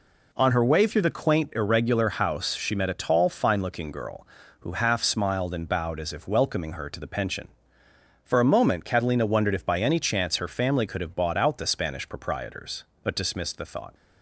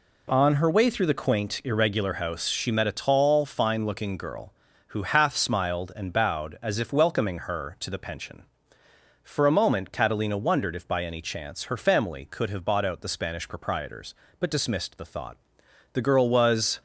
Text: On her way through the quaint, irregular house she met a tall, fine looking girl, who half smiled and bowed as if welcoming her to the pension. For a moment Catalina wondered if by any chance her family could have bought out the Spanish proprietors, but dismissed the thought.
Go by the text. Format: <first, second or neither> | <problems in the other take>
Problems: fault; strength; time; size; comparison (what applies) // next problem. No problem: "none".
first | goes on to say "The girl was"; noticeable; from 15.9 s on; 0.86 s long